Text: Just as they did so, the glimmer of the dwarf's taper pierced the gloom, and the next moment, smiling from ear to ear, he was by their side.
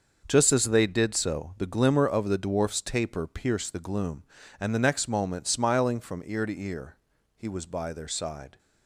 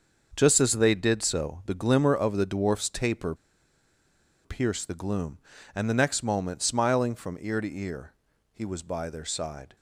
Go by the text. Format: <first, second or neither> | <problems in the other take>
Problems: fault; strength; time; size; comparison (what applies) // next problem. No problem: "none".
first | starts louder than the rest; until 1.3 s; 6.5 dB; also in the first // pauses between "taper" and "pierced"; at 3.3 s; 1.1 s long